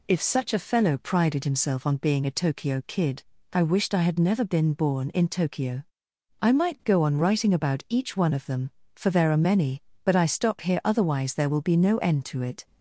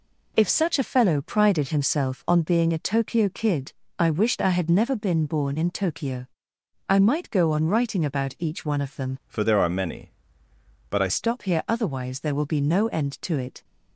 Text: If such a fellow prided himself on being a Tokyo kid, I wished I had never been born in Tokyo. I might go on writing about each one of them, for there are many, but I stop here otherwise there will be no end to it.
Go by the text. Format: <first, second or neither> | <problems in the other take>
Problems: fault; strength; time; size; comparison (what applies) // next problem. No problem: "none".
first | changes voice from "for" to "I"; from 9.2 to 11.0 s; 1.8 s long